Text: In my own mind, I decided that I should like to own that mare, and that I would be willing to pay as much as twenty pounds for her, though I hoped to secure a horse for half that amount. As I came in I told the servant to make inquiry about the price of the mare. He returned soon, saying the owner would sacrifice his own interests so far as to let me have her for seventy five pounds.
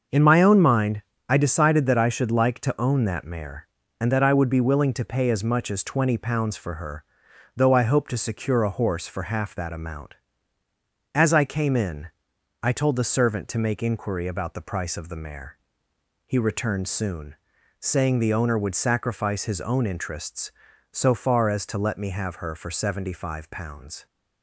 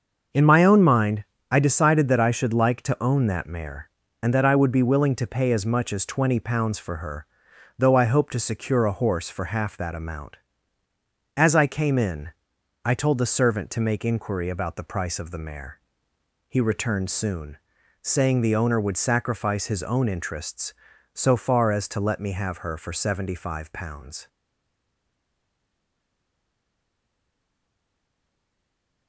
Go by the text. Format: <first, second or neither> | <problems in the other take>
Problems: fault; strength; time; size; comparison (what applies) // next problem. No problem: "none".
first | starts louder than the rest; until 1.6 s; 6.5 dB; also in the first // pauses between "in" and "I"; noticeable; at 12.2 s; 0.54 s long; noticeable in the first // stays silent after the last word; strong; from 24.2 s on; 4.8 s long